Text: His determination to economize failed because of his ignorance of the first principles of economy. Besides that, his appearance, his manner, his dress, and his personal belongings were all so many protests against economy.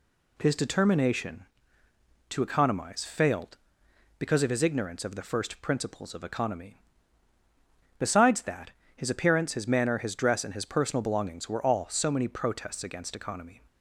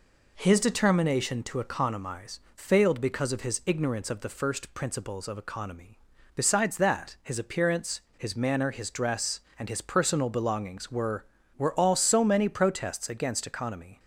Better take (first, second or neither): first